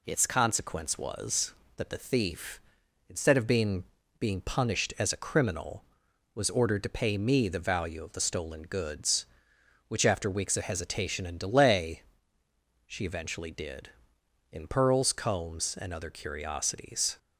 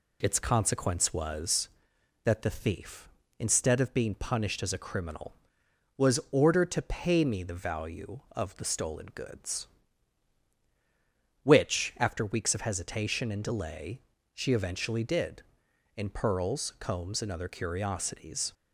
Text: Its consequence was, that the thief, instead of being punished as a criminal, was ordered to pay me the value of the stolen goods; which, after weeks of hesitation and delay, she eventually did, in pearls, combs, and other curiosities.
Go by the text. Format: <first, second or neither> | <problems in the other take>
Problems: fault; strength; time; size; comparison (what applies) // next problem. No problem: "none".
second | says "being" twice; at 4.1 s